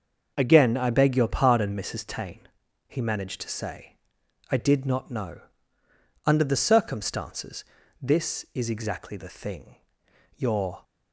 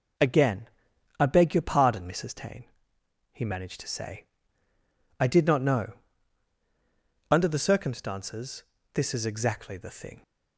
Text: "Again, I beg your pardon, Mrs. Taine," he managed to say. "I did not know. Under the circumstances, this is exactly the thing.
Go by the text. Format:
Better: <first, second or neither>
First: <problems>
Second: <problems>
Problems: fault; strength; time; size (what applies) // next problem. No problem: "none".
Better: second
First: starts louder than the rest; until 1.3 s; 6 dB // goes on to say "Your"; slight; from 10.3 s on; 0.46 s long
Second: none